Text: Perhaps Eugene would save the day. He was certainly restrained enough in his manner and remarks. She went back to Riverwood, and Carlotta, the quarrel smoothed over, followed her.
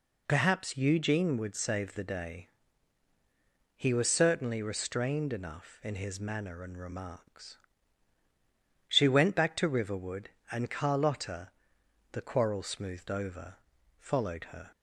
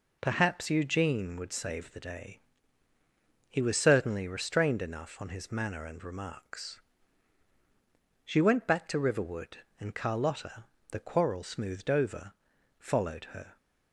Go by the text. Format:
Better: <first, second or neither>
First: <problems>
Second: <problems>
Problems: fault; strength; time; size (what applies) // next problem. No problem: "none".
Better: first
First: none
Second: says "on" for "in"; at 5.2 s